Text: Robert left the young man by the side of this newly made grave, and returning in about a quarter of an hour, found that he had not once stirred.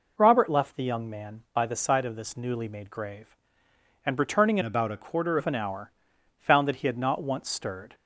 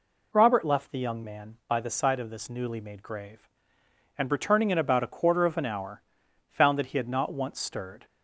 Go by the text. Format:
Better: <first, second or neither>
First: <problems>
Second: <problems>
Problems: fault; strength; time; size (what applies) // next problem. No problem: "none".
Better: second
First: changes voice from "about" to "quarter"; from 4.6 to 5.3 s; 0.7 s long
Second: none